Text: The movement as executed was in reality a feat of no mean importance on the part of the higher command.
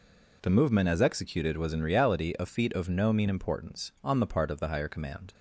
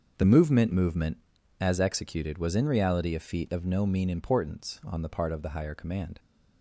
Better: first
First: none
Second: starts louder than the rest; until 1.1 s; 6 dB // says "movement" twice; at 0.7 s

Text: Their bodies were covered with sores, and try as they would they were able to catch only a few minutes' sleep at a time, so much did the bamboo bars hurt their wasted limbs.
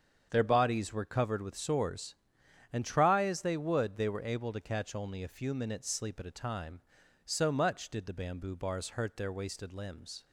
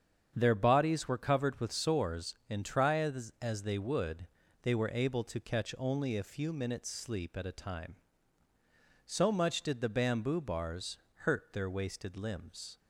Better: first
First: starts louder than the rest; strong; until 1.3 s; 7.5 dB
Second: starts louder than the rest; strong; until 1.3 s; 7.5 dB // says "as" twice; at 3.4 s // pauses between "would" and "they"; slight; at 4.2 s; 0.36 s long // pauses between "bars" and "hurt"; slight; at 10.9 s; 0.20 s long

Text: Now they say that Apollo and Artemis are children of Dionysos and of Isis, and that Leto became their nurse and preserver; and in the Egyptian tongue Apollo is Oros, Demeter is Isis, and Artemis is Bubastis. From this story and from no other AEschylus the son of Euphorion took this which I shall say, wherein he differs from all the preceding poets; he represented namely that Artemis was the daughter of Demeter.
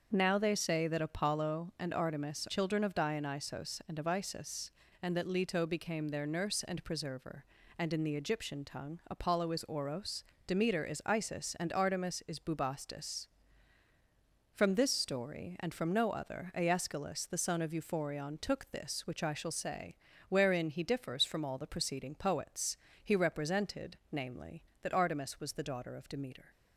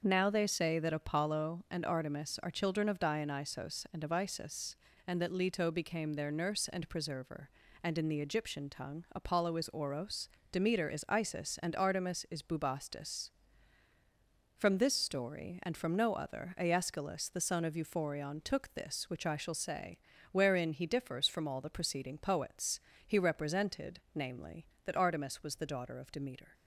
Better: second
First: starts louder than the rest; until 1.1 s; 6.5 dB // skips "are"; at 2.4 s // pauses between "represented" and "namely"; slight; at 23.9 s; 0.16 s long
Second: starts louder than the rest; until 1.0 s; 6.5 dB // pauses between "represented" and "namely"; slight; at 23.9 s; 0.16 s long

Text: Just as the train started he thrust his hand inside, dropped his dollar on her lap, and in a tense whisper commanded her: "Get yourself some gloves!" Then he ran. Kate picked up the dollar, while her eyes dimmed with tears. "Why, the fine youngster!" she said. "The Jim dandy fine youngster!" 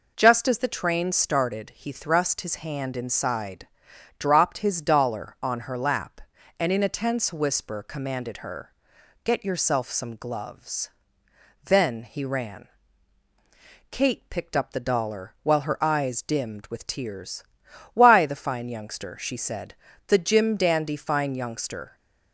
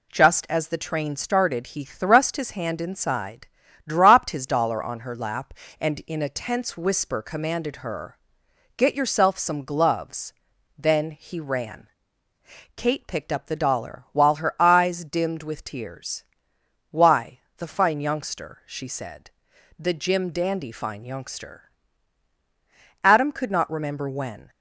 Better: first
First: none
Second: goes on to say "Adam could not remember when"; from 23.0 s on; 1.4 s long

